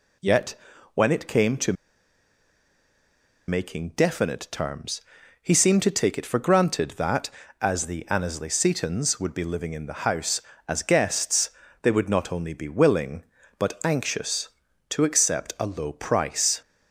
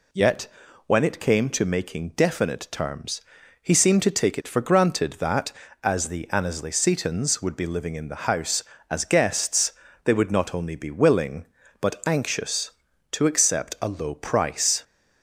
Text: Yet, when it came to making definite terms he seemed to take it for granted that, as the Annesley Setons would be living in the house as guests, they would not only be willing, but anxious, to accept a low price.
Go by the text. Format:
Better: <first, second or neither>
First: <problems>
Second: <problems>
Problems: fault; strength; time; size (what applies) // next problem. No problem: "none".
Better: second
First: pauses between "to" and "making"; strong; at 1.7 s; 1.7 s long // pauses between "terms" and "he"; at 5.0 s; 0.42 s long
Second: pauses between "terms" and "he"; at 3.2 s; 0.42 s long